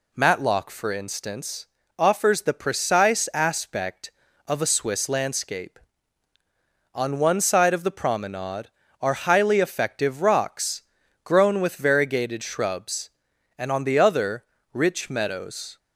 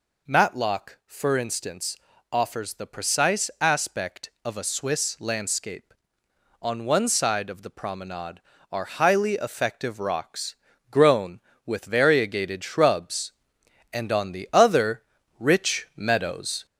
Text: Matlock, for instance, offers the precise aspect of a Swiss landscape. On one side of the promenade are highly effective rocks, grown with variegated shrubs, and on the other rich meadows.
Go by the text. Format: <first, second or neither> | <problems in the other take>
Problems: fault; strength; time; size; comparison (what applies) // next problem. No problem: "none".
first | gets louder; slight; throughout; 2.5 dB // pauses between "other" and "rich"; slight; at 15.0 s; 0.36 s long; slight in the first